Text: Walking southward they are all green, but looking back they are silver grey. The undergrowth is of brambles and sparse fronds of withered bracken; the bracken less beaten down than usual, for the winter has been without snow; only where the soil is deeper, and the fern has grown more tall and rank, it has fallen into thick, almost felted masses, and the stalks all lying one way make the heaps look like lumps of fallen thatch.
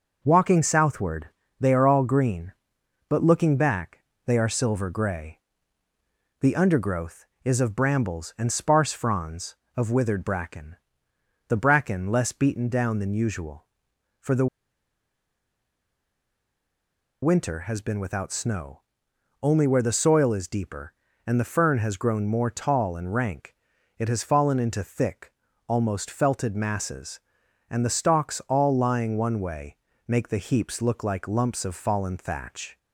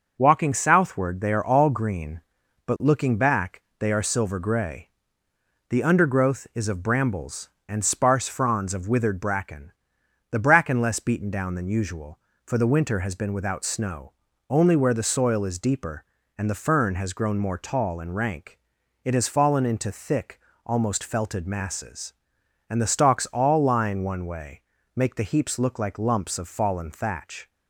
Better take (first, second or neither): second